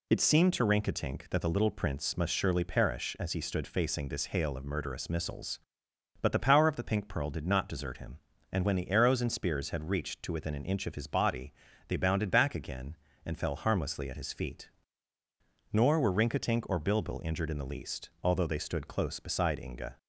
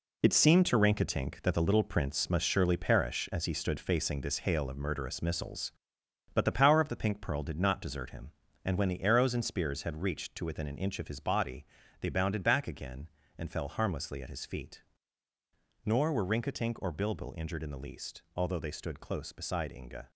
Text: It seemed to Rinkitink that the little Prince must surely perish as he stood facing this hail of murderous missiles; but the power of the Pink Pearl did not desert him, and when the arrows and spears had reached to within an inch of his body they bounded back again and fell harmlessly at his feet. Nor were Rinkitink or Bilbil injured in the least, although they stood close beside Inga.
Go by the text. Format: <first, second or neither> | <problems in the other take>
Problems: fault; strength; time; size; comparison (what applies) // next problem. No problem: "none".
first | gets quieter; strong; throughout; 9 dB // pauses between "body" and "they"; slight; at 11.6 s; 0.36 s long; slight in the first